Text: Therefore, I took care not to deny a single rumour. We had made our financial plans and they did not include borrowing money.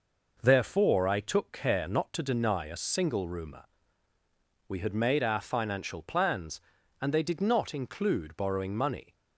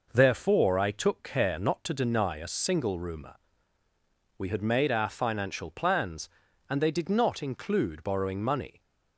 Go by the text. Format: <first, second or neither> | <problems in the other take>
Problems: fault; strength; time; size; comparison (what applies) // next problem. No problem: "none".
neither | none